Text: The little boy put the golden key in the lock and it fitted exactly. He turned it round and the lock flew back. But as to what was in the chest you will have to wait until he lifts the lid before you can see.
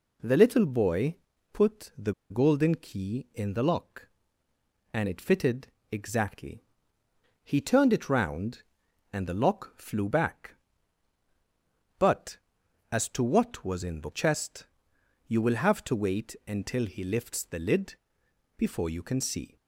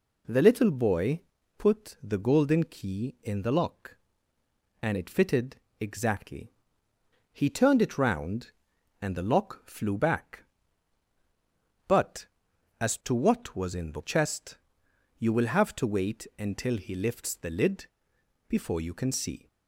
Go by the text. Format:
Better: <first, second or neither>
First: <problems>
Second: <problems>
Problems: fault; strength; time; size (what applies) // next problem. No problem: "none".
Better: second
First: pauses between "boy" and "put"; at 1.1 s; 0.38 s long // pauses between "the" and "golden"; slight; at 2.1 s; 0.18 s long // pauses between "fitted" and "exactly"; slight; at 5.6 s; 0.24 s long // pauses between "chest" and "you"; noticeable; at 14.6 s; 0.60 s long // pauses between "lid" and "before"; noticeable; at 17.9 s; 0.64 s long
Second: pauses between "boy" and "put"; at 1.1 s; 0.38 s long // pauses between "fitted" and "exactly"; slight; at 5.5 s; 0.24 s long // pauses between "chest" and "you"; noticeable; at 14.5 s; 0.60 s long // pauses between "lid" and "before"; noticeable; at 17.8 s; 0.64 s long